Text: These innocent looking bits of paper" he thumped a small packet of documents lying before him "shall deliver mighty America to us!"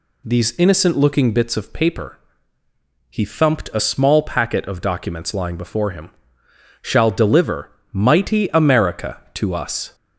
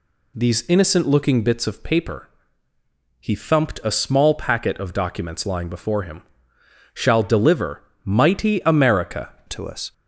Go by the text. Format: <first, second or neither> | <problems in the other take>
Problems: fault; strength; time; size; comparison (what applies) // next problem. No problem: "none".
first | pauses between "paper" and "he"; noticeable; at 2.2 s; 0.94 s long; noticeable in the first // pauses between "him" and "shall"; noticeable; at 6.2 s; 0.70 s long; noticeable in the first // pauses between "deliver" and "mighty"; slight; at 7.8 s; 0.22 s long; slight in the first // changes voice at "to"; from 9.4 s on; 0.5 s long